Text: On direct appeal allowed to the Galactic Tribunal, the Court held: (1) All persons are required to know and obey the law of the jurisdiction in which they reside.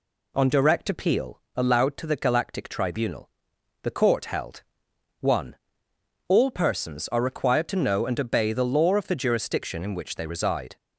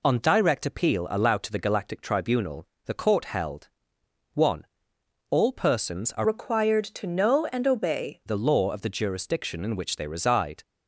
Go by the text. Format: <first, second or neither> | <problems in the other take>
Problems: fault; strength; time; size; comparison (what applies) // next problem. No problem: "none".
first | changes voice from "required" to "obey"; from 6.2 to 8.2 s; 2.0 s long